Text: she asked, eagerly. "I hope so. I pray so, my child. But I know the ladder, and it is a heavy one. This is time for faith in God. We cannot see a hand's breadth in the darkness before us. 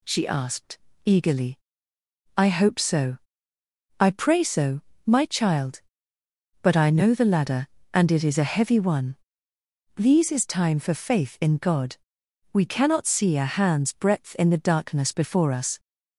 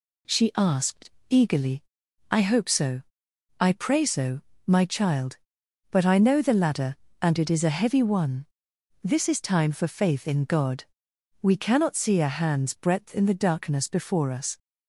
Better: second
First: says "These" for "This"; at 9.9 s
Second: none

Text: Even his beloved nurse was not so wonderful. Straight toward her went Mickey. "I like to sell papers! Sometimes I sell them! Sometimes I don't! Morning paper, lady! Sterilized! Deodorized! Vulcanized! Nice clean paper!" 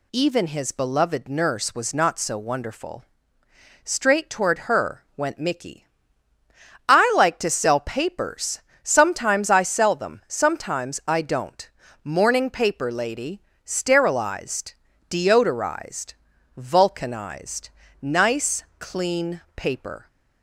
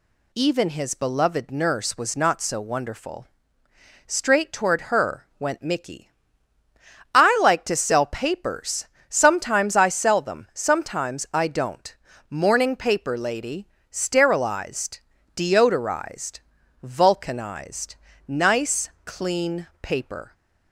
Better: neither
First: none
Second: none

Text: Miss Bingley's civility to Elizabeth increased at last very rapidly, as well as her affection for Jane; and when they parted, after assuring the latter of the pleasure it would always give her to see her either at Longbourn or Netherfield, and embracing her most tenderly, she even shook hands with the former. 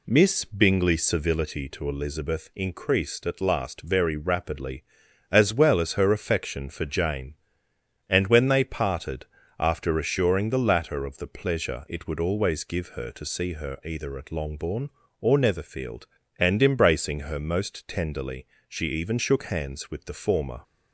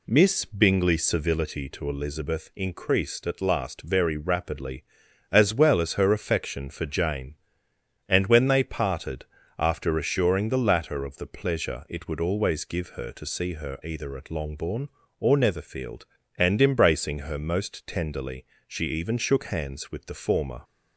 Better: neither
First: none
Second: none

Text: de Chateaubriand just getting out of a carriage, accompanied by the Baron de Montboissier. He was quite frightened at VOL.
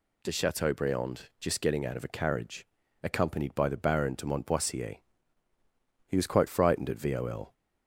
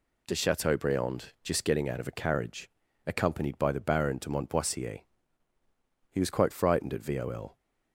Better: first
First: none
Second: gets quieter; noticeable; throughout; 5 dB

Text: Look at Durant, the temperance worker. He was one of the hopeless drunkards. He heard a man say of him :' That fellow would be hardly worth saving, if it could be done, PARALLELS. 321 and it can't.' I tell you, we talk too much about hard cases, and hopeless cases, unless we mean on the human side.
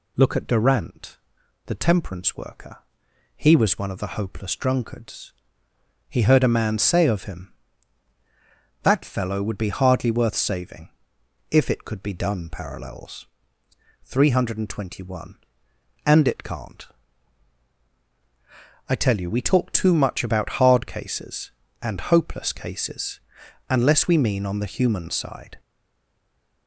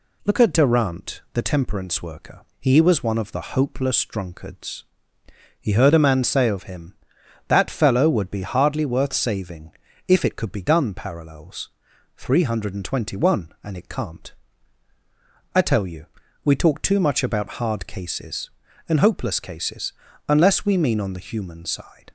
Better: second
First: stays silent after the last word; from 25.5 s on; 1.1 s long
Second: none

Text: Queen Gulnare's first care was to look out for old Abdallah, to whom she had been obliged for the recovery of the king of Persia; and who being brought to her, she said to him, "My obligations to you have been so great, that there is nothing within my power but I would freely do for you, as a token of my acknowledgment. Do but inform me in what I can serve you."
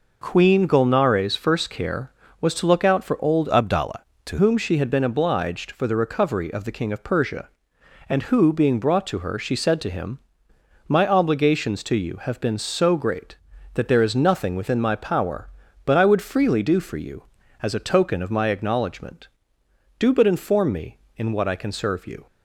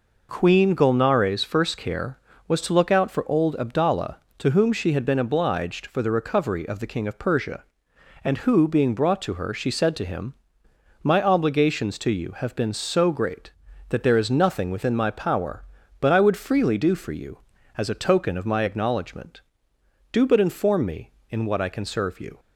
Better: second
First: changes voice from "Abdallah" to "to"; from 3.5 to 4.3 s; 0.8 s long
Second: none

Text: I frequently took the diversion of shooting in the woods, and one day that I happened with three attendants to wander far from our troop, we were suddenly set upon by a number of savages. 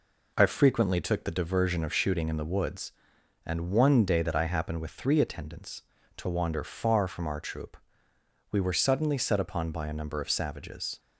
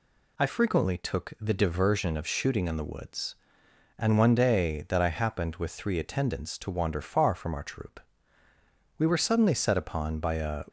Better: first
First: none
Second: stops before "number of savages"; at 10.6 s

